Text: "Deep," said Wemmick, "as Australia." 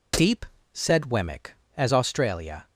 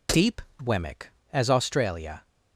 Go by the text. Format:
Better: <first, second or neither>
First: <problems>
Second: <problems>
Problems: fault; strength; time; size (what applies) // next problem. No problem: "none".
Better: first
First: none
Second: skips "said"; at 0.5 s